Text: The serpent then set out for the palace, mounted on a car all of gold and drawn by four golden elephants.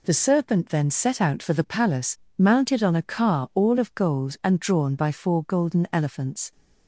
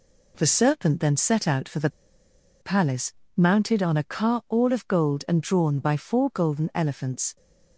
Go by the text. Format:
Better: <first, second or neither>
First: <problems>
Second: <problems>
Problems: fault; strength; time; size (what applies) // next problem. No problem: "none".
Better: first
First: none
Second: pauses between "the" and "palace"; noticeable; at 1.8 s; 0.71 s long